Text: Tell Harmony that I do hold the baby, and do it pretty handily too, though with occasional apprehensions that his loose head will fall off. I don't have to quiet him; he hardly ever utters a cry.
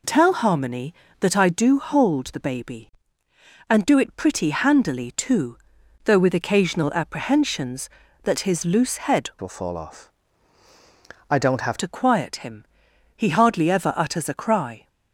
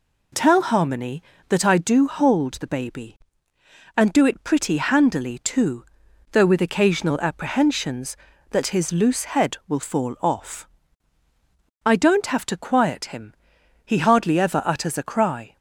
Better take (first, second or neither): second